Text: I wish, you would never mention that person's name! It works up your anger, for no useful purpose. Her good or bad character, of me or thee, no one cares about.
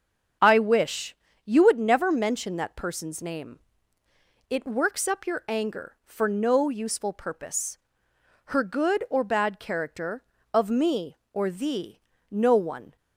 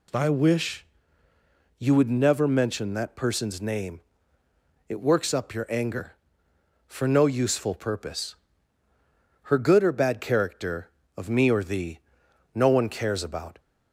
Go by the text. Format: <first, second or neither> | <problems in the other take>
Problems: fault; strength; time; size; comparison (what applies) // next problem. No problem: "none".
second | starts louder than the rest; strong; until 1.7 s; 7.5 dB // stops before "cares about"; at 12.9 s